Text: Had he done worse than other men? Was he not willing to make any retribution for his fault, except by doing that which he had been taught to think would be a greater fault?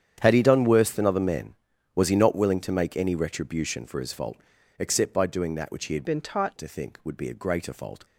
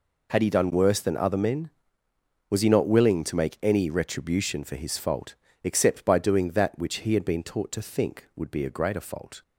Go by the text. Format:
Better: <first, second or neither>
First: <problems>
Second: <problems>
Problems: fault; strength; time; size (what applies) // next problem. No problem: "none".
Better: second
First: starts louder than the rest; strong; until 1.2 s; 9 dB // changes voice from "been" to "taught"; from 6.0 to 6.5 s; 0.5 s long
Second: none